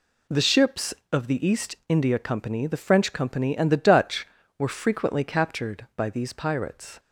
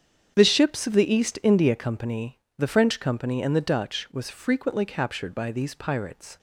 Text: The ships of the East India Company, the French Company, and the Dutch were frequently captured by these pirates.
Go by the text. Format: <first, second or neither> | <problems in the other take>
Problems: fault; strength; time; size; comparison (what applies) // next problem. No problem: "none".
first | starts louder than the rest; strong; until 1.3 s; 8 dB // says "was" for "were"; at 4.1 s